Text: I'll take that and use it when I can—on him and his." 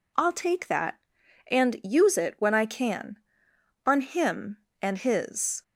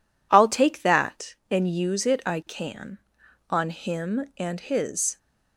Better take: first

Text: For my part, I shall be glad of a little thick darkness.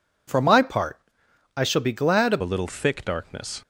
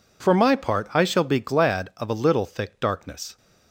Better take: second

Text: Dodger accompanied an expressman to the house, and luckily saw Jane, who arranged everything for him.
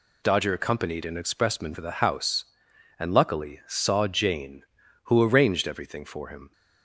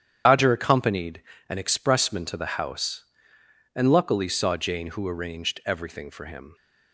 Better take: first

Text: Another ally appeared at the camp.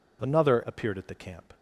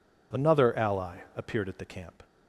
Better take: second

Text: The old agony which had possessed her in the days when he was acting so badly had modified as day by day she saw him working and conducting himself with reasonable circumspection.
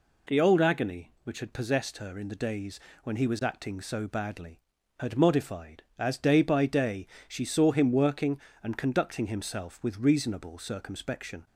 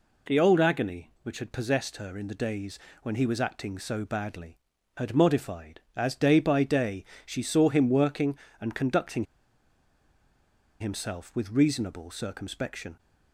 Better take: first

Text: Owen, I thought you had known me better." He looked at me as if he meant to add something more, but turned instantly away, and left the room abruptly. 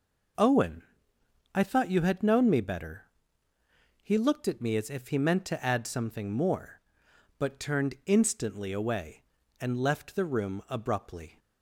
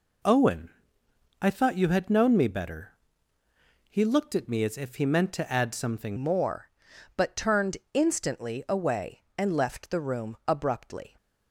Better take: first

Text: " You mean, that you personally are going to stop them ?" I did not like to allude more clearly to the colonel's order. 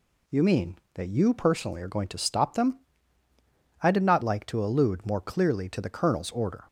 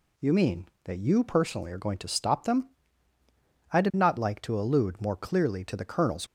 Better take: first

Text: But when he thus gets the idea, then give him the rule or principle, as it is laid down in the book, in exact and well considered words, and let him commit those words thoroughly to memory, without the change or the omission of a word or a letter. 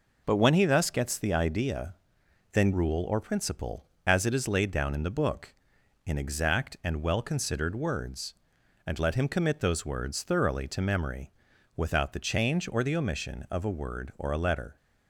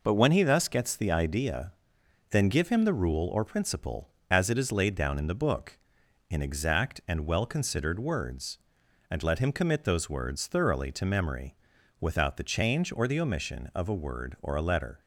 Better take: second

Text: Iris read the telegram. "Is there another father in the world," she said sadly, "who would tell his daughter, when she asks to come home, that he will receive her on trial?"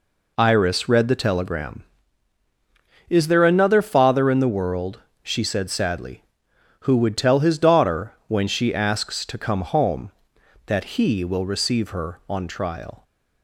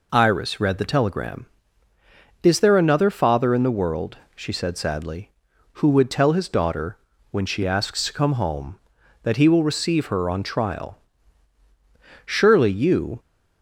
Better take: first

